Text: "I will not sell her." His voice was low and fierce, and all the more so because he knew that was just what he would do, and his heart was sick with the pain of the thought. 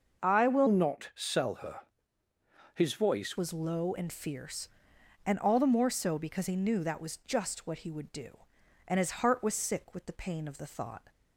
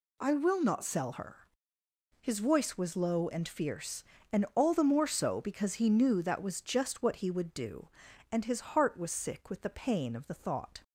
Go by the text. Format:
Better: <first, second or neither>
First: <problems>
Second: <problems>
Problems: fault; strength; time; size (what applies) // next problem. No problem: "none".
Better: second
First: changes voice from "not" to "voice"; from 0.6 to 3.3 s; 2.7 s long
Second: none